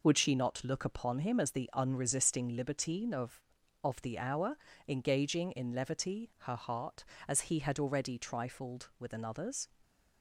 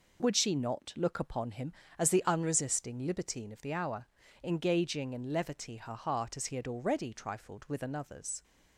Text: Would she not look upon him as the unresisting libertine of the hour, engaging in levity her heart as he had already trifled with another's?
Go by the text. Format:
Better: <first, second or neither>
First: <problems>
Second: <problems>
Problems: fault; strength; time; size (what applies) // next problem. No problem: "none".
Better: second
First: says "of" twice; at 3.8 s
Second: none